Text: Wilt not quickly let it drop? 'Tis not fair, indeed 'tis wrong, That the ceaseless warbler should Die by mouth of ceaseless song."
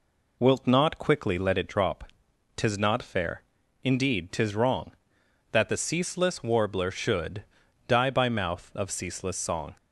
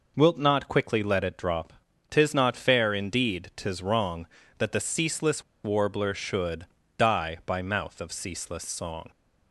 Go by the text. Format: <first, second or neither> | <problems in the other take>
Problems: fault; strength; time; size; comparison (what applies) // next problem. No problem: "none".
first | pauses between "ceaseless" and "warbler"; slight; at 5.4 s; 0.22 s long // pauses between "should" and "Die"; slight; at 6.6 s; 0.32 s long; also in the first